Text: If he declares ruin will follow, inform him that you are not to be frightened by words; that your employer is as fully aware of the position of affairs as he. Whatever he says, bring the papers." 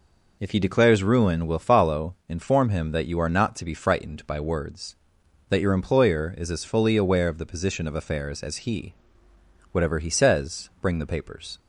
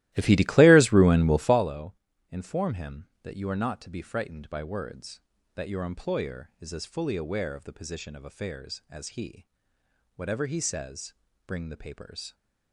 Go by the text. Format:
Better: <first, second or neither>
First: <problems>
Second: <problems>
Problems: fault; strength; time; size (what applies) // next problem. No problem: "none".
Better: first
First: none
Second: starts louder than the rest; strong; until 1.7 s; 16 dB